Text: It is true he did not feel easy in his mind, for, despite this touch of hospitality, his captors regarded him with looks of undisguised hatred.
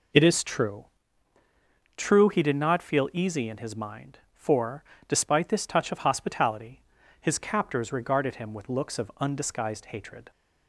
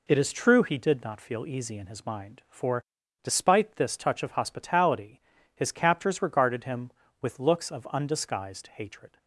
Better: second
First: says "true" twice; at 1.9 s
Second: none

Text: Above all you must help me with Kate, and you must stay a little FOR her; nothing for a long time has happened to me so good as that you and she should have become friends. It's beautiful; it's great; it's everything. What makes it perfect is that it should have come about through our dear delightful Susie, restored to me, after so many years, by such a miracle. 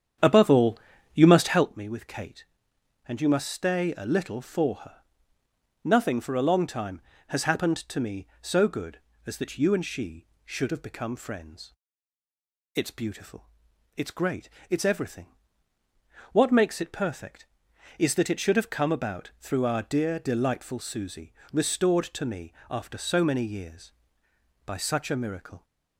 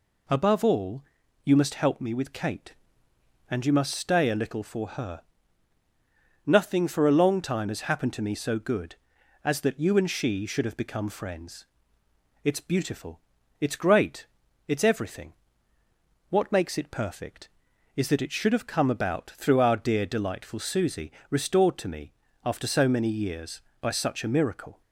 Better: second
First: starts louder than the rest; strong; until 1.7 s; 9 dB // pauses between "all" and "you"; slight; at 0.7 s; 0.36 s long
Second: pauses between "all" and "you"; at 1.0 s; 0.42 s long

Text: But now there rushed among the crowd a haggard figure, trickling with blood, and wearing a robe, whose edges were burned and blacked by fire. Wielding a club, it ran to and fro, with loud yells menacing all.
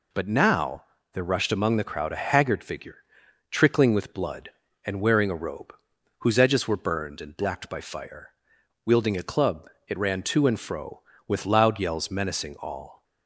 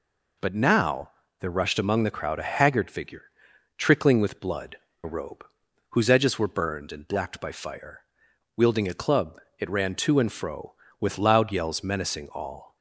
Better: first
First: pauses between "now" and "there"; slight; at 0.8 s; 0.30 s long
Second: pauses between "now" and "there"; slight; at 1.0 s; 0.30 s long // skips "and wearing"; at 4.8 s

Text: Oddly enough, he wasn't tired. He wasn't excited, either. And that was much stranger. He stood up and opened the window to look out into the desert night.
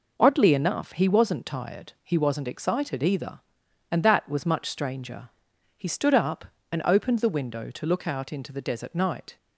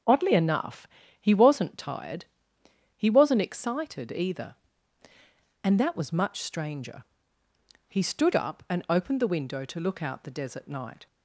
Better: first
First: none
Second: starts louder than the rest; until 1.4 s; 6.5 dB // skips "into"; at 10.2 s

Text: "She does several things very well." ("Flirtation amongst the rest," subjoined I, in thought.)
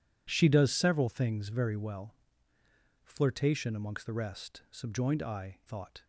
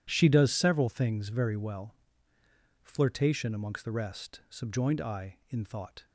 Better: second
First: skips "in"; at 5.6 s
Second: none

